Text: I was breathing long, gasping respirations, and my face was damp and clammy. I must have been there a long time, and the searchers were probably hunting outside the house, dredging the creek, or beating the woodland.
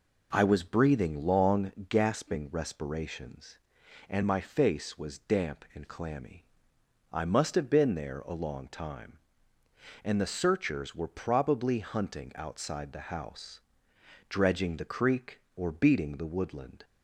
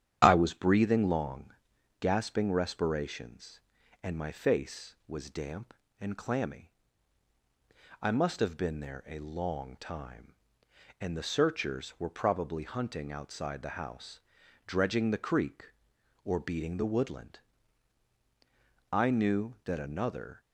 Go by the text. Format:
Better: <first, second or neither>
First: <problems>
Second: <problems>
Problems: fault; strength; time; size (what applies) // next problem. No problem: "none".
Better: first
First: none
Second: starts louder than the rest; strong; until 1.2 s; 9.5 dB // goes on to say "I knew that another"; from 18.9 s on; 1.5 s long